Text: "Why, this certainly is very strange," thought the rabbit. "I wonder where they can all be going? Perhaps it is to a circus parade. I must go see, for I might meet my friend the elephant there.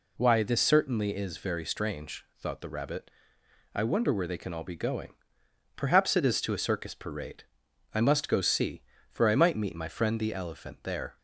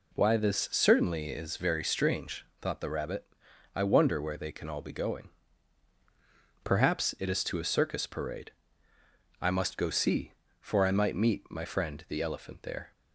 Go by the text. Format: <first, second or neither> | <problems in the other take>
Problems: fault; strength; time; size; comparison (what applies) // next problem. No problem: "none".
neither | none